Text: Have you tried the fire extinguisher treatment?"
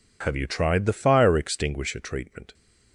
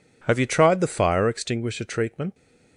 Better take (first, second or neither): neither